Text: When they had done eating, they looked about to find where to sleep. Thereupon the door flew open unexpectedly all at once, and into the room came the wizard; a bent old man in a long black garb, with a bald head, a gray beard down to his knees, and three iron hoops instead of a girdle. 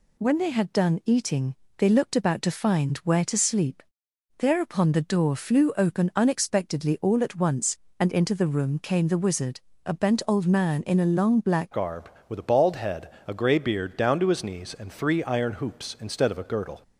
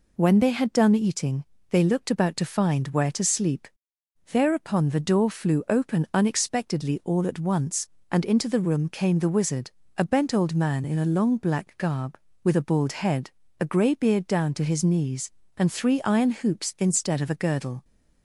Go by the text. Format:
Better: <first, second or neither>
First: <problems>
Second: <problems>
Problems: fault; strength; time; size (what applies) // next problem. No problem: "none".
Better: second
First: changes voice at "garb"; from 11.7 s on; 5.1 s long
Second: none